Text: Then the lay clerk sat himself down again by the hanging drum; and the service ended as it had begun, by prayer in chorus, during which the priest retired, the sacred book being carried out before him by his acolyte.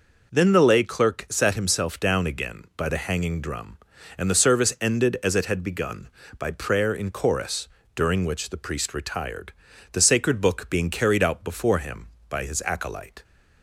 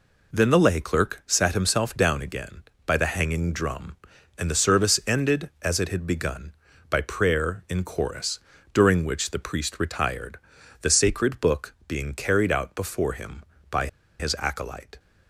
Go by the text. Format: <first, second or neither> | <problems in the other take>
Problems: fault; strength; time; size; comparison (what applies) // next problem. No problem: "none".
first | pauses between "by" and "his"; slight; at 13.8 s; 0.32 s long